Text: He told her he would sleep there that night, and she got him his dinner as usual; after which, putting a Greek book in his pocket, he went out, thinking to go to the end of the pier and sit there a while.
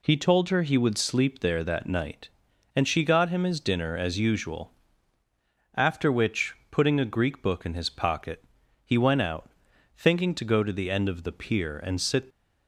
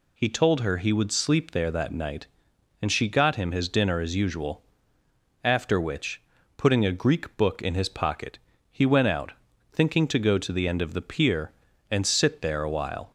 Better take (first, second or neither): second